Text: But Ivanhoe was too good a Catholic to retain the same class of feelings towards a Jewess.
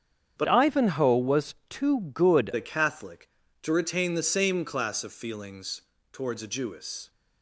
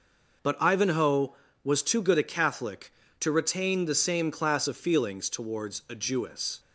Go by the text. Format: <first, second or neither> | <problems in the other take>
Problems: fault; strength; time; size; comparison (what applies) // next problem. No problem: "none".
second | starts louder than the rest; strong; until 1.3 s; 8 dB // changes voice from "Ivanhoe" to "good"; from 0.4 to 2.5 s; 2.1 s long // pauses between "feelings" and "towards"; slight; at 5.8 s; 0.30 s long